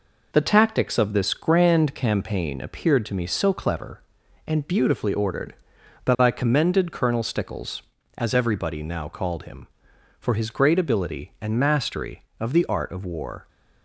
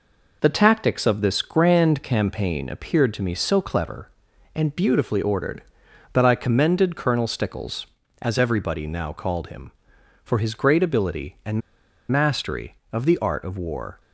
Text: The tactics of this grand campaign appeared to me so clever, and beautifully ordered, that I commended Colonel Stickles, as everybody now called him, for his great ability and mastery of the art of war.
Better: first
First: none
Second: pauses between "and" and "mastery"; noticeable; at 11.6 s; 0.51 s long

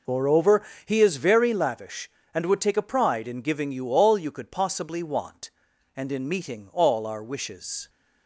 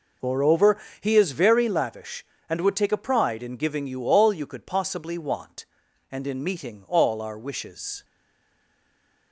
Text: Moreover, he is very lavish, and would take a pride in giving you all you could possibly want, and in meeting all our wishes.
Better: first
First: none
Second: stays silent after the last word; noticeable; from 8.0 s on; 1.3 s long

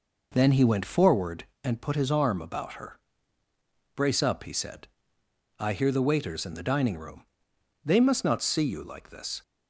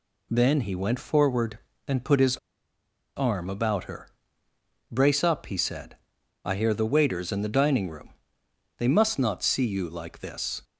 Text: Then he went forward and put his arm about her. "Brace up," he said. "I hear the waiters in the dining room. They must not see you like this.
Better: first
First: none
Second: pauses between "his" and "arm"; noticeable; at 2.3 s; 0.79 s long

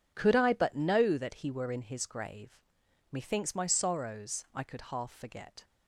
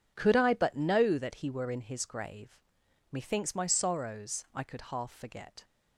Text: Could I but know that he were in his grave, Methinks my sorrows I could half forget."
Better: neither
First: none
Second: none

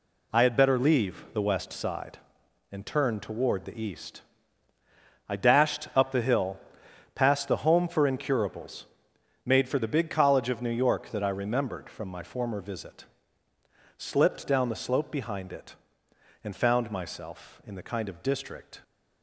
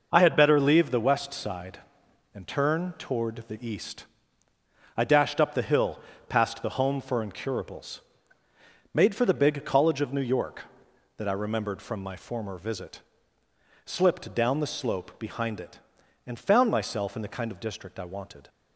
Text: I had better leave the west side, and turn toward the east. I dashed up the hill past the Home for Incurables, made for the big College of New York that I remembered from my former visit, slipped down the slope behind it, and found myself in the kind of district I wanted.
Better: second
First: pauses between "hill" and "past"; noticeable; at 6.5 s; 0.56 s long // stops before "I wanted"; at 18.8 s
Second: pauses between "hill" and "past"; slight; at 5.9 s; 0.30 s long

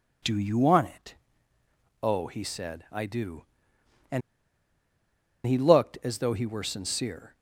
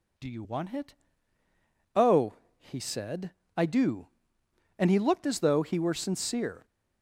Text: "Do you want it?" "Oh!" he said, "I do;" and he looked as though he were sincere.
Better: second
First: pauses between "and" and "he"; strong; at 4.2 s; 1.2 s long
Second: none

